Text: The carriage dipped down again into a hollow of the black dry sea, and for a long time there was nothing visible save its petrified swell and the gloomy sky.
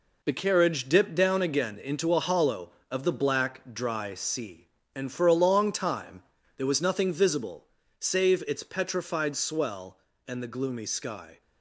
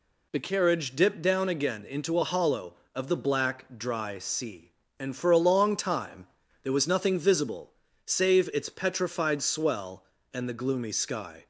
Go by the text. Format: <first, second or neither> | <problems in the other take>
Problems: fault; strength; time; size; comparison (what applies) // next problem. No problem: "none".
second | gets quieter; throughout; 7 dB // pauses between "time" and "there"; at 6.2 s; 0.36 s long; also in the second // pauses between "visible" and "save"; slight; at 7.6 s; 0.36 s long; slight in the second